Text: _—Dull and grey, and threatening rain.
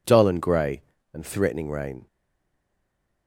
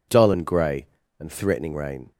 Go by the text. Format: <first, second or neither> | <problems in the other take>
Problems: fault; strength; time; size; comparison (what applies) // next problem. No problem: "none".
second | stays silent after the last word; noticeable; from 2.0 s on; 1.2 s long